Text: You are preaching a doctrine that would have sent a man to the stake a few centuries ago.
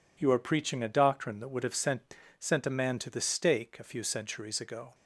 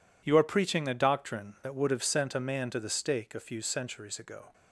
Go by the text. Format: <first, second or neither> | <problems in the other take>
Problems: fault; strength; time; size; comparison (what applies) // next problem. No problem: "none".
second | says "sent" twice; at 2.4 s